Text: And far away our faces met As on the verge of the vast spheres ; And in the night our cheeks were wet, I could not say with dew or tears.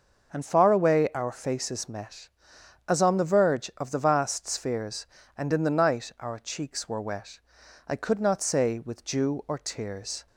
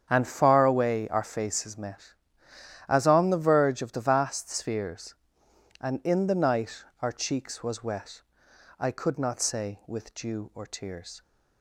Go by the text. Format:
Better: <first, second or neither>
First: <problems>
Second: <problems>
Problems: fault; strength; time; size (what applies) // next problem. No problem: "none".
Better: first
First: starts louder than the rest; noticeable; until 1.3 s; 6 dB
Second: starts louder than the rest; strong; until 1.1 s; 8 dB // pauses between "night" and "our"; slight; at 6.8 s; 0.18 s long // says "was" for "were"; at 7.6 s